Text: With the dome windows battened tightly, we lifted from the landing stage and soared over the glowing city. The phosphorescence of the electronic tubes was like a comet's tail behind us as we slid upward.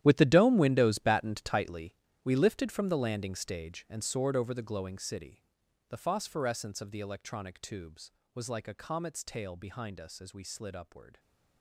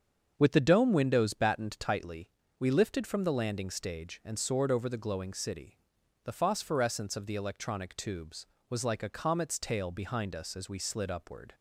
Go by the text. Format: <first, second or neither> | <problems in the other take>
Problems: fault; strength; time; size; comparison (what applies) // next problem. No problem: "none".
second | gets quieter; strong; throughout; 15.5 dB // starts louder than the rest; strong; until 1.0 s; 11.5 dB; also in the second